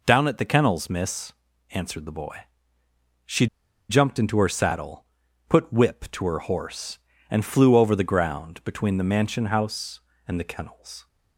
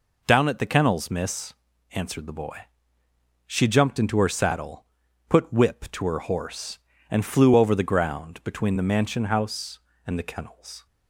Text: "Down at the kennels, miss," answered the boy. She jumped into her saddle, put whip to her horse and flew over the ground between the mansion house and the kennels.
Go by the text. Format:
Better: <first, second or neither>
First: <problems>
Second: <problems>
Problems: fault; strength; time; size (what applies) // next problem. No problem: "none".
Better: second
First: pauses between "She" and "jumped"; at 3.4 s; 0.43 s long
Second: none